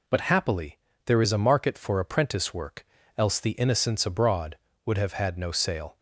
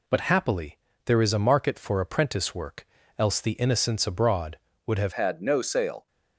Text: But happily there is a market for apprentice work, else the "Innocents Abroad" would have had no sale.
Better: first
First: pauses between "happily" and "there"; slight; at 0.7 s; 0.28 s long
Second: pauses between "happily" and "there"; slight; at 0.7 s; 0.28 s long // changes voice at "had"; from 5.1 s on; 0.9 s long

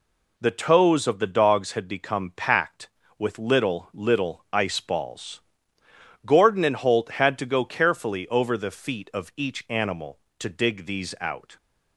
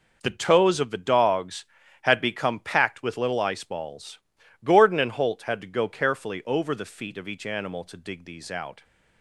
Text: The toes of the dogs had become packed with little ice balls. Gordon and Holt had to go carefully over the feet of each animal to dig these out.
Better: second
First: says "little" twice; at 3.9 s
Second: none

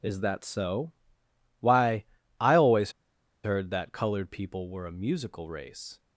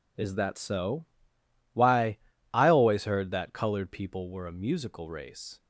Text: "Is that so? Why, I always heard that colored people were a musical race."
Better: second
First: pauses between "always" and "heard"; noticeable; at 2.9 s; 0.51 s long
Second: none

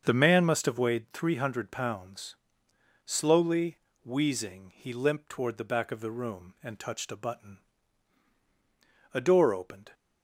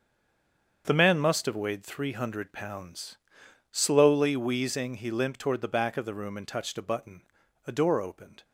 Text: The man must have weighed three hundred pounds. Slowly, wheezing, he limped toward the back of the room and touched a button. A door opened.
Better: first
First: starts louder than the rest; until 1.0 s; 7 dB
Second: stays silent before the first word; slight; until 0.8 s; 0.8 s long // starts louder than the rest; until 1.8 s; 7 dB

